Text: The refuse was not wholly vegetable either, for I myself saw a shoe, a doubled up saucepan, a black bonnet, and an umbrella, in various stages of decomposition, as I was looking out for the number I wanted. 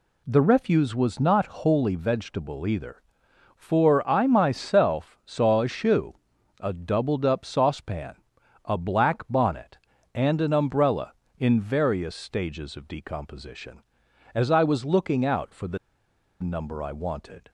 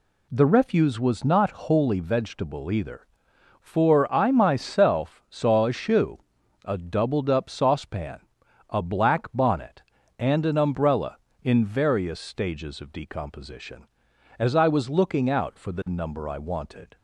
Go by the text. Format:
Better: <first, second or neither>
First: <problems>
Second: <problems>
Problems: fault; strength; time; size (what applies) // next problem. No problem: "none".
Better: second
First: pauses between "the" and "number"; noticeable; at 15.7 s; 0.64 s long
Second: none